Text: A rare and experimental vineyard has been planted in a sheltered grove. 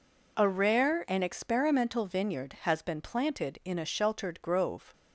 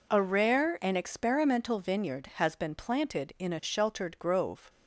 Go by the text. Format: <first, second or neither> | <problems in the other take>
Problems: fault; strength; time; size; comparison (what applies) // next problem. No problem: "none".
neither | none